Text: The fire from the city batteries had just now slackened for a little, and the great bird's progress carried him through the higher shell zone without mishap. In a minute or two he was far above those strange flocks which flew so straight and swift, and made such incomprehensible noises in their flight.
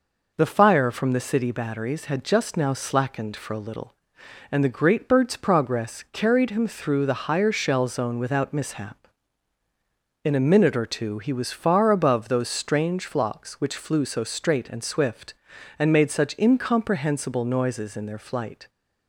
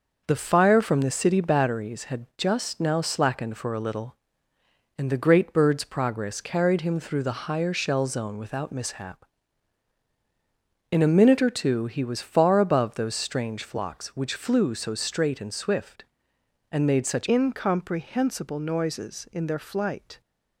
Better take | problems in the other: first | starts louder than the rest; noticeable; until 1.2 s; 6 dB // changes voice at "incomprehensible"; from 17.2 s on; 3.0 s long

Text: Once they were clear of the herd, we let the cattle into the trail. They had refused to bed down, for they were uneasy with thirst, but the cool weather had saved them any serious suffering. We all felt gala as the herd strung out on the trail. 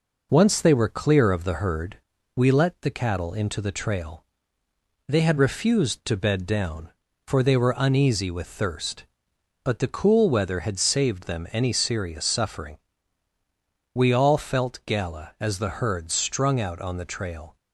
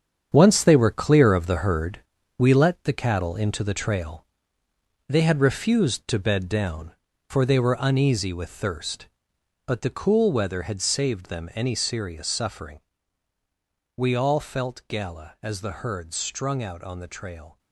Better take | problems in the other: first | gets quieter; strong; throughout; 9.5 dB

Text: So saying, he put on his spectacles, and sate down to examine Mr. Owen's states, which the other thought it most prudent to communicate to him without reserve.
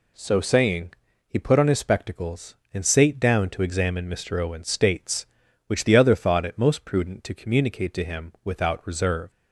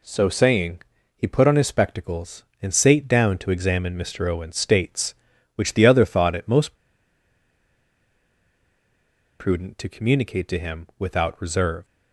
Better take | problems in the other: first | pauses between "most" and "prudent"; strong; at 6.7 s; 2.6 s long

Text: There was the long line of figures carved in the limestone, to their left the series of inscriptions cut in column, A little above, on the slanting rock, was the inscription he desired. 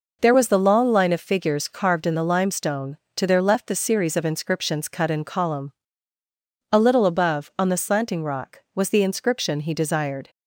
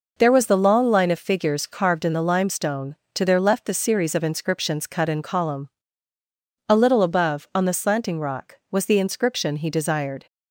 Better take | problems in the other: neither | none

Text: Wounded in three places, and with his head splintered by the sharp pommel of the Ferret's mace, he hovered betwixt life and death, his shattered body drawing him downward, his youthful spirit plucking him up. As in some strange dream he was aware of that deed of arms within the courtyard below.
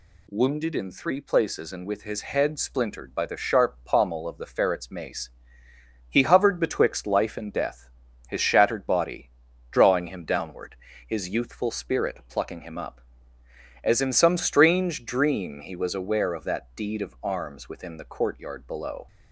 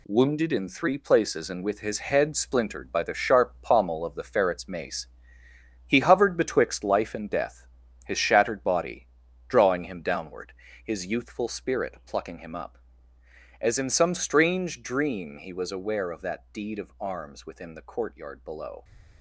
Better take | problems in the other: first | gets quieter; strong; throughout; 7.5 dB // pauses between "body" and "drawing"; at 9.0 s; 0.40 s long; also in the first

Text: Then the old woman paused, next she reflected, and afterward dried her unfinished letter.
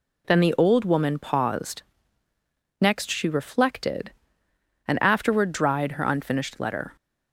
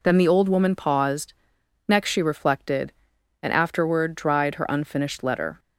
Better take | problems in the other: neither | none

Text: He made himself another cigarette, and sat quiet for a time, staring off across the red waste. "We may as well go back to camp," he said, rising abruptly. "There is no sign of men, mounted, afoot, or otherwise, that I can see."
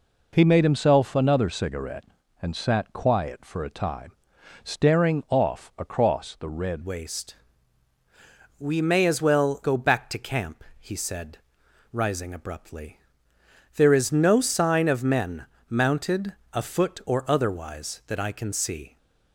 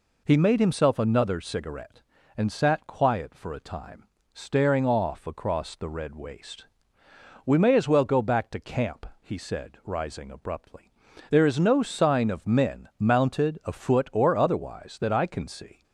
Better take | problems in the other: second | changes voice at "waste"; from 6.8 s on; 12.1 s long

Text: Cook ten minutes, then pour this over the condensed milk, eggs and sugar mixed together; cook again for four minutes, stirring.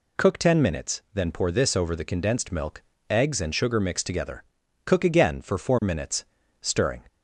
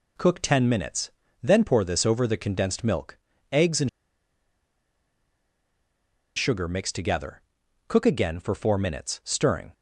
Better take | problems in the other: first | pauses between "and" and "sugar"; strong; at 3.8 s; 2.4 s long

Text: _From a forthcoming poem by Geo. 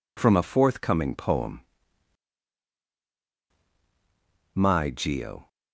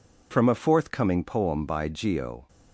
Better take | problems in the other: second | says "my" for "by"; at 4.5 s

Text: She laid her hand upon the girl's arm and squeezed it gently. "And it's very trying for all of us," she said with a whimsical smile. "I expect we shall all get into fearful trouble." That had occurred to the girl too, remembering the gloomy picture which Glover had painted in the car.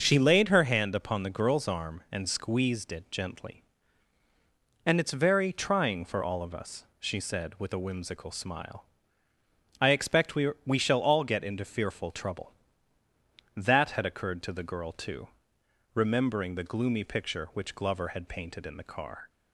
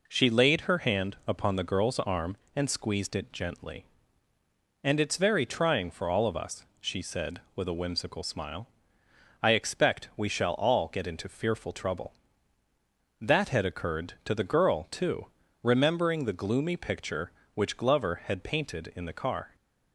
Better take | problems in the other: second | starts louder than the rest; noticeable; until 1.0 s; 6 dB // says "we" twice; at 10.6 s

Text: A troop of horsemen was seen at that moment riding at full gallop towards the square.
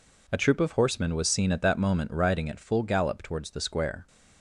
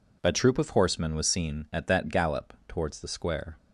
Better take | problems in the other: first | skips "moment riding at full"; at 2.0 s

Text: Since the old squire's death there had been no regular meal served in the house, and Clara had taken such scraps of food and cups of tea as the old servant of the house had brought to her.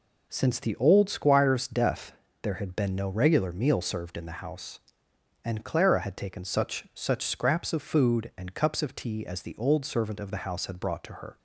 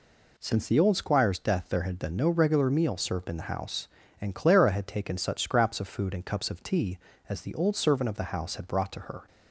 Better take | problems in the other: second | pauses between "death" and "there"; slight; at 2.1 s; 0.30 s long // says "such" twice; at 6.9 s

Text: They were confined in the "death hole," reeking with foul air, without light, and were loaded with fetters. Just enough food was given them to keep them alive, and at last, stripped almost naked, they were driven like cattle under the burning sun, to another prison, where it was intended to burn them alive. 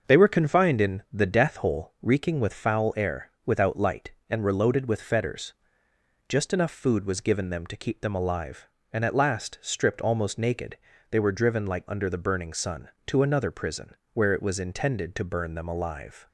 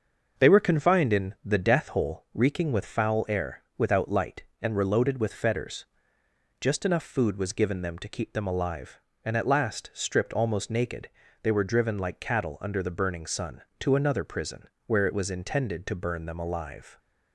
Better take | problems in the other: second | starts louder than the rest; until 1.1 s; 6.5 dB; also in the second // skips "cattle"; at 11.8 s

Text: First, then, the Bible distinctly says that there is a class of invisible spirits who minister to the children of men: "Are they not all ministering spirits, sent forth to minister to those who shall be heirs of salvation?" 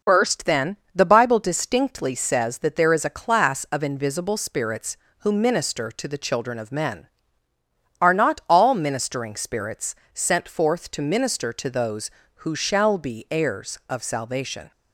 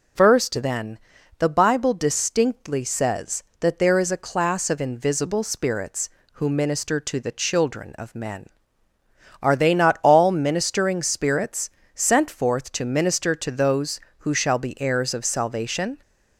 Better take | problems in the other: second | skips "they"; at 8.1 s

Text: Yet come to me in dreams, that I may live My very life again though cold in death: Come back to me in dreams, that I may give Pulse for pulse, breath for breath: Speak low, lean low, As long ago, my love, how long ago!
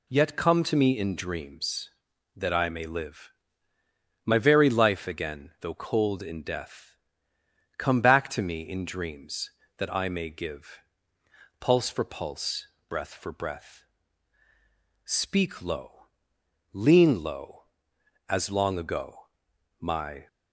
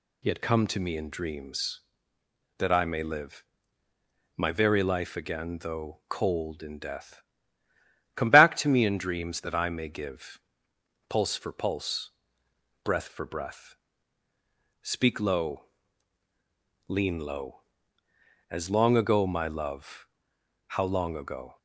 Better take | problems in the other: second | pauses between "live" and "My"; noticeable; at 3.3 s; 0.92 s long; noticeable in the second // pauses between "give" and "Pulse"; noticeable; at 10.7 s; 0.80 s long; noticeable in the second // stops before "love how long ago"; at 20.2 s

